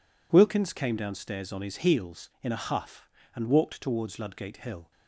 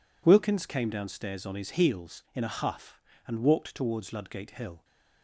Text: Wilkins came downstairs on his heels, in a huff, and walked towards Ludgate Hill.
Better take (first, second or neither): neither